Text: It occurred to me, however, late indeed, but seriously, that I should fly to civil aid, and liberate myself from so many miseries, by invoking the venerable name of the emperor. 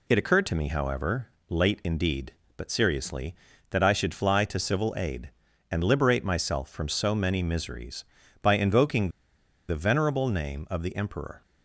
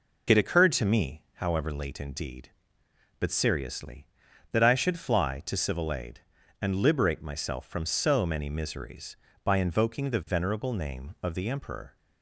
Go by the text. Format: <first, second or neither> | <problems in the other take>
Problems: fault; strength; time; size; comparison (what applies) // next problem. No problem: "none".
second | pauses between "invoking" and "the"; noticeable; at 9.0 s; 0.58 s long